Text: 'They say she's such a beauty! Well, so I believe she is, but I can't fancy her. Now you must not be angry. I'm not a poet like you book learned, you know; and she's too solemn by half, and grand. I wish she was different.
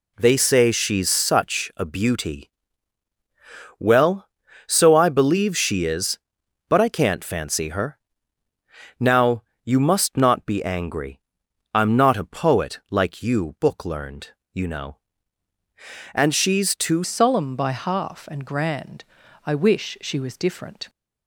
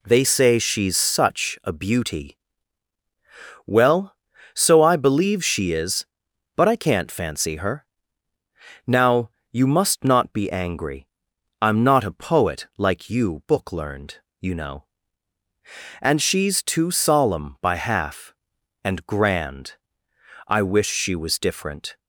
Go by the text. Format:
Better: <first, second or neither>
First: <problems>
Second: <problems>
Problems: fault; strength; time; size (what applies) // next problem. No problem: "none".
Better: second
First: pauses between "Now" and "you"; slight; at 9.4 s; 0.22 s long // changes voice at "solemn"; from 17.0 s on; 3.8 s long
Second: pauses between "Now" and "you"; slight; at 9.2 s; 0.22 s long